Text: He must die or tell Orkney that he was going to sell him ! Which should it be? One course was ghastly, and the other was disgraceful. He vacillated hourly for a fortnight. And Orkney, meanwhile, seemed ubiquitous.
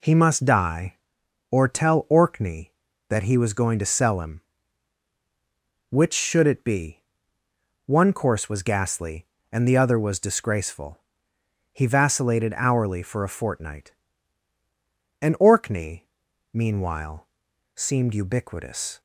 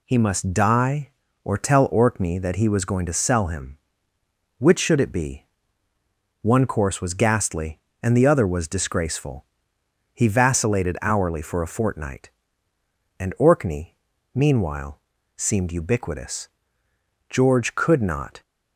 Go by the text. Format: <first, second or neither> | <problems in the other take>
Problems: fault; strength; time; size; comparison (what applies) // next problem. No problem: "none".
first | goes on to say "George could not"; noticeable; from 17.2 s on; 1.1 s long